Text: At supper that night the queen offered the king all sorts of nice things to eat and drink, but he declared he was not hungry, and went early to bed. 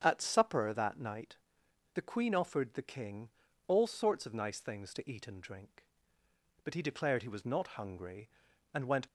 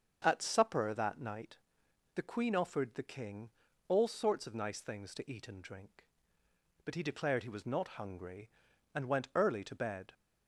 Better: second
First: starts louder than the rest; strong; until 1.0 s; 7.5 dB // pauses between "night" and "the"; noticeable; at 1.3 s; 0.58 s long // pauses between "king" and "all"; at 3.2 s; 0.40 s long // stops before "early to bed"; at 9.0 s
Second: starts louder than the rest; until 1.2 s; 6.5 dB // pauses between "night" and "the"; noticeable; at 1.5 s; 0.58 s long // pauses between "king" and "all"; at 3.4 s; 0.40 s long

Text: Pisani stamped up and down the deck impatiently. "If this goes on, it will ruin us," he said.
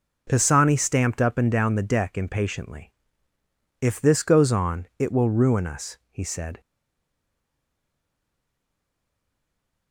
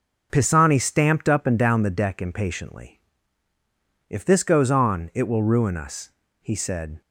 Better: second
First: stays silent after the last word; strong; from 6.6 s on; 3.3 s long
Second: none

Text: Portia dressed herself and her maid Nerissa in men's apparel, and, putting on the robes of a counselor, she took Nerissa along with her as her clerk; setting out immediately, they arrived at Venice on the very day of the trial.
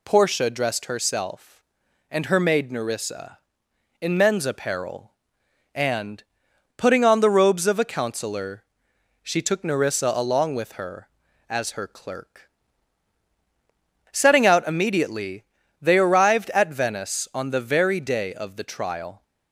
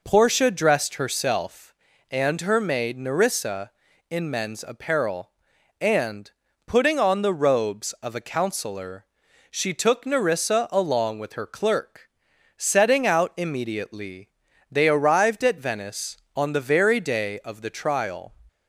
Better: first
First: none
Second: skips "as her"; at 11.4 s

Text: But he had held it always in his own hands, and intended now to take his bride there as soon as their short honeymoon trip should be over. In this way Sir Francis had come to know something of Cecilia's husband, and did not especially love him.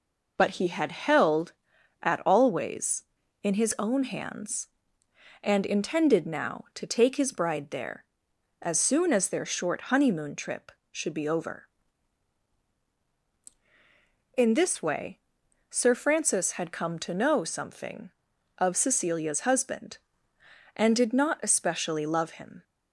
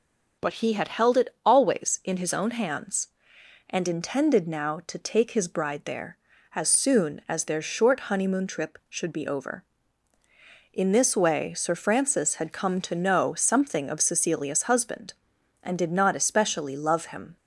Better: second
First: says "at" for "it"; at 2.0 s // pauses between "way" and "Sir"; noticeable; at 15.1 s; 0.50 s long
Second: none

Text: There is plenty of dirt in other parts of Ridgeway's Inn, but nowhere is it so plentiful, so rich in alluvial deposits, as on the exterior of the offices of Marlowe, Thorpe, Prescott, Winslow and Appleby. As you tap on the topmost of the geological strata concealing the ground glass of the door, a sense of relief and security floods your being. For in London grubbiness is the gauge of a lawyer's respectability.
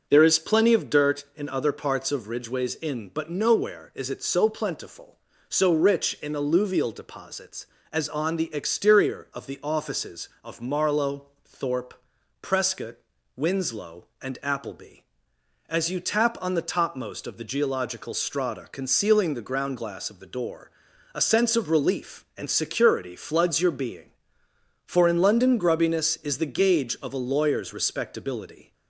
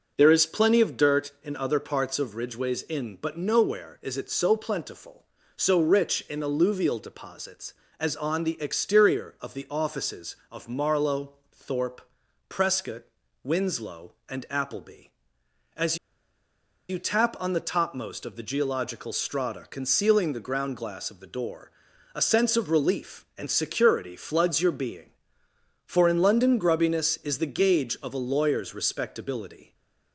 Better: first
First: none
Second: pauses between "As" and "you"; noticeable; at 15.9 s; 0.92 s long // stays silent after the last word; slight; from 29.6 s on; 0.5 s long

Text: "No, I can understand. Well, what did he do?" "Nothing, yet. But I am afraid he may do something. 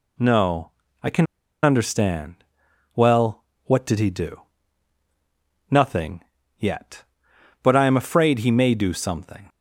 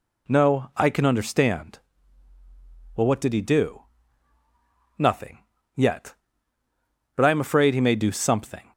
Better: second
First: pauses between "can" and "understand"; at 1.2 s; 0.37 s long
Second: none

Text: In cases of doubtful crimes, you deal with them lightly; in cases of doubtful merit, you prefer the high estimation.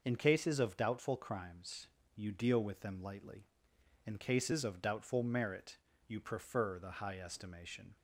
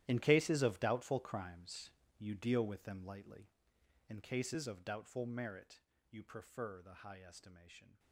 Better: first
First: none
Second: gets quieter; strong; throughout; 16.5 dB

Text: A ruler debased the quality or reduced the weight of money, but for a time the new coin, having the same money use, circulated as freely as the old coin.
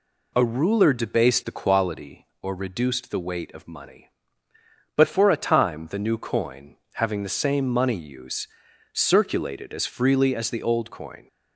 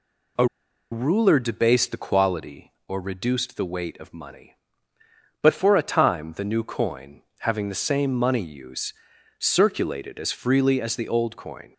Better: first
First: none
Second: pauses between "A" and "ruler"; noticeable; at 0.4 s; 0.46 s long

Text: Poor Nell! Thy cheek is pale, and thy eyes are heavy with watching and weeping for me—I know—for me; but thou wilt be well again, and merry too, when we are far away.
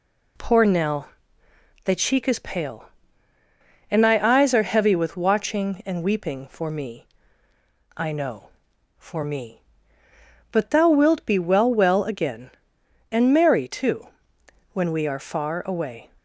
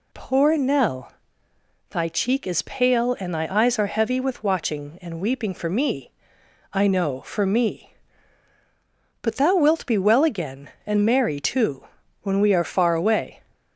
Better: second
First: says "well" twice; at 11.7 s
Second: none

